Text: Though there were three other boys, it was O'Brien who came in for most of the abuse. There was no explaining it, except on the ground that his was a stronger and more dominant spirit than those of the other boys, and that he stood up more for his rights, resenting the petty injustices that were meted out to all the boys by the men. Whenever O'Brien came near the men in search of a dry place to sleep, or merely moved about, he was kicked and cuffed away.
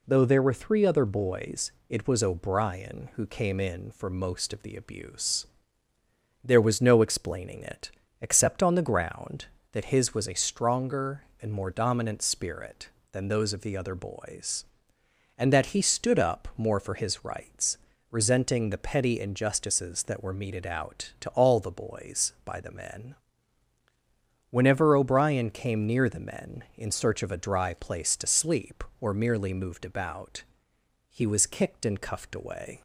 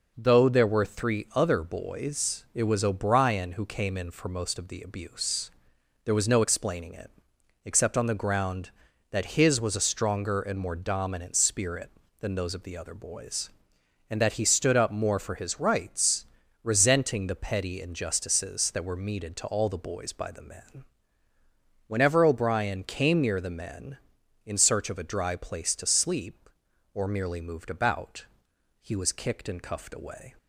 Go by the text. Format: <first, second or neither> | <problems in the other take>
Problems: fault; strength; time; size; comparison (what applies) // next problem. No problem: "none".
first | skips "out"; at 19.3 s